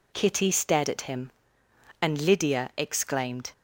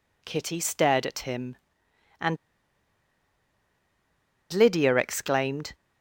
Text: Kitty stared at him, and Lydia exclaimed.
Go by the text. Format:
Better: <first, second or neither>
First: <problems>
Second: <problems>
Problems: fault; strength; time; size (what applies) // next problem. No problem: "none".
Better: first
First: none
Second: pauses between "and" and "Lydia"; strong; at 2.3 s; 2.1 s long